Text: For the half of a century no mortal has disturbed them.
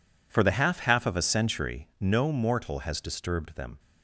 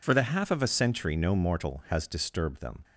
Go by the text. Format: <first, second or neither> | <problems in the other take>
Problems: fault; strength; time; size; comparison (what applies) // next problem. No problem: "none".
second | says "half" twice; at 0.7 s